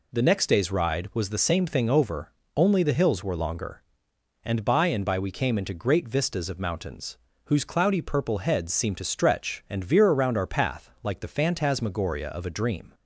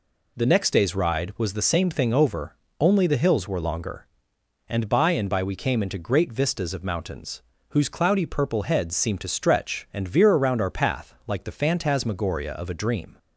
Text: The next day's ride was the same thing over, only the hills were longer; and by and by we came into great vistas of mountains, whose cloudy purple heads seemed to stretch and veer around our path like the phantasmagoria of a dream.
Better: neither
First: none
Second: none

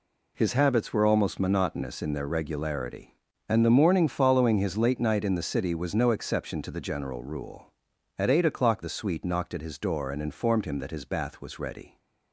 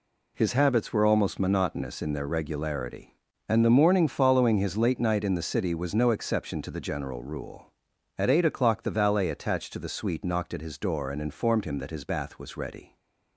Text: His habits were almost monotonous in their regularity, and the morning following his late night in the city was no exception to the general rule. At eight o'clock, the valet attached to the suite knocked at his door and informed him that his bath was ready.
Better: second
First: skips "the valet attached to"; at 8.8 s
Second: none

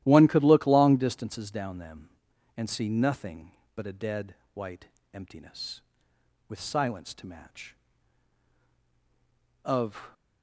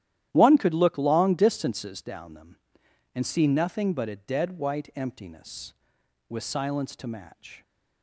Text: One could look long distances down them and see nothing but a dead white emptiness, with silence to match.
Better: second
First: starts louder than the rest; strong; until 1.0 s; 13 dB // pauses between "dead" and "white"; slight; at 4.3 s; 0.18 s long // pauses between "white" and "emptiness"; slight; at 4.8 s; 0.26 s long // goes on to say "Of"; from 9.6 s on; 0.50 s long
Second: starts louder than the rest; strong; until 1.3 s; 12 dB

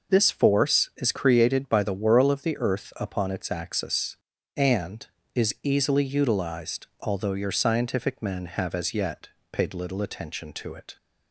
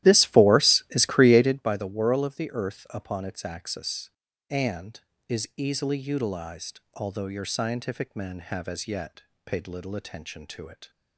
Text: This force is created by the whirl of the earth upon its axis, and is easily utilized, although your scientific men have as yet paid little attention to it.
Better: first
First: pauses between "yet" and "paid"; slight; at 9.2 s; 0.24 s long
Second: starts louder than the rest; strong; until 1.7 s; 14 dB // pauses between "yet" and "paid"; slight; at 9.2 s; 0.24 s long

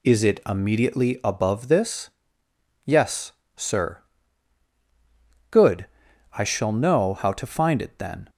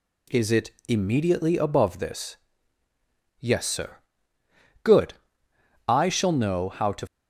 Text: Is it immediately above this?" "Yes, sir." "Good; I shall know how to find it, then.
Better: first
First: none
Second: stops before "find it then"; at 7.0 s

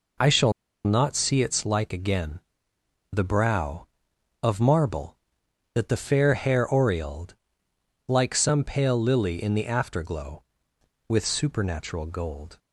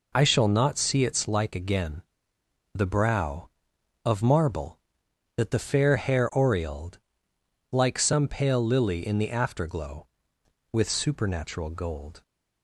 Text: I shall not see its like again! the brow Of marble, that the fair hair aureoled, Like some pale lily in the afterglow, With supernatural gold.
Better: second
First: pauses between "shall" and "not"; slight; at 0.5 s; 0.32 s long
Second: none

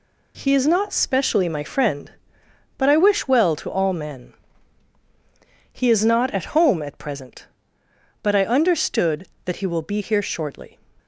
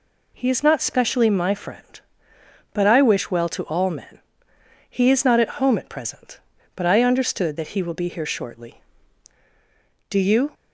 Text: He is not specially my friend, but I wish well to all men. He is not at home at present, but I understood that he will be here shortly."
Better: first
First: none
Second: goes on to say "Do you"; slight; from 10.0 s on; 0.42 s long

